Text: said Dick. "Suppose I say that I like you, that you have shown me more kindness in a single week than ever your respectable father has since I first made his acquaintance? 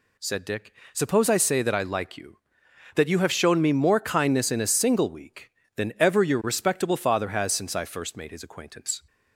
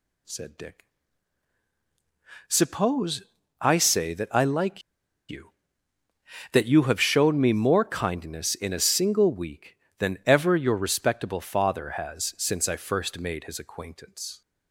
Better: first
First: none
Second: pauses between "Suppose" and "I"; at 3.2 s; 0.40 s long // pauses between "like" and "you"; noticeable; at 4.8 s; 0.47 s long

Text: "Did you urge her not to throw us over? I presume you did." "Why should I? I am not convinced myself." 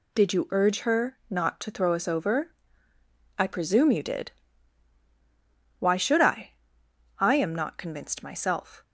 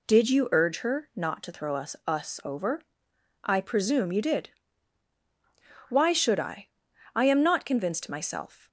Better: first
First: none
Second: says "us" twice; at 2.0 s

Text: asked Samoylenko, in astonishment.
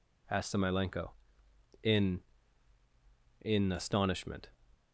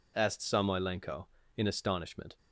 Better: second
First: says "in" twice; at 3.4 s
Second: none

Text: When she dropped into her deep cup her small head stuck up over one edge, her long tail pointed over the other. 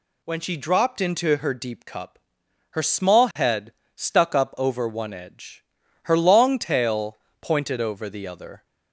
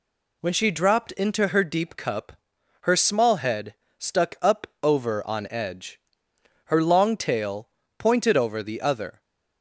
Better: first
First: pauses between "cup" and "her"; noticeable; at 2.1 s; 0.54 s long // pauses between "head" and "stuck"; slight; at 3.7 s; 0.22 s long // pauses between "tail" and "pointed"; slight; at 7.1 s; 0.22 s long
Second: pauses between "cup" and "her"; noticeable; at 2.3 s; 0.50 s long // pauses between "head" and "stuck"; slight; at 3.7 s; 0.25 s long // pauses between "up" and "over"; slight; at 4.6 s; 0.20 s long // says "on" for "one"; at 5.2 s // pauses between "tail" and "pointed"; slight; at 7.6 s; 0.28 s long

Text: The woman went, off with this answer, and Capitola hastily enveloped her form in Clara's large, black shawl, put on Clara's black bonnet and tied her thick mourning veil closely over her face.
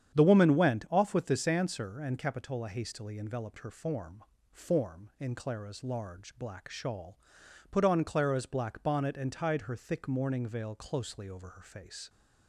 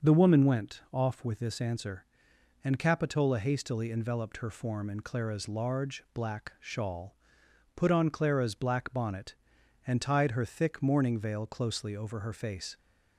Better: second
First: starts louder than the rest; strong; until 1.2 s; 9 dB // says "form" twice; at 4.5 s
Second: starts louder than the rest; until 1.1 s; 6 dB

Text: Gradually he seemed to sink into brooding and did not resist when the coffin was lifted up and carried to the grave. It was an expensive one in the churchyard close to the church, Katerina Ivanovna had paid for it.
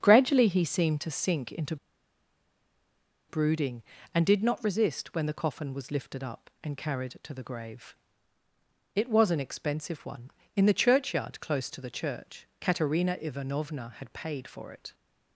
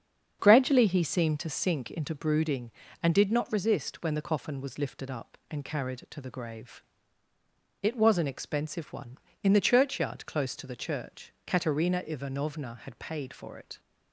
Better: second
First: starts louder than the rest; strong; until 1.0 s; 7.5 dB // pauses between "into" and "brooding"; strong; at 1.7 s; 1.5 s long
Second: starts louder than the rest; strong; until 1.4 s; 7.5 dB

